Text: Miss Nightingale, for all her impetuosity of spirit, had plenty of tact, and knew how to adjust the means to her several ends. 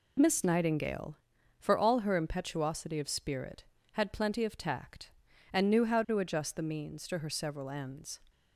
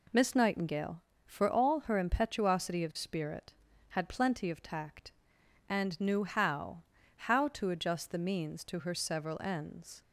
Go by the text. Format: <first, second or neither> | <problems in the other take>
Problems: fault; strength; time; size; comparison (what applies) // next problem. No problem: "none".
first | says "how" twice; at 7.1 s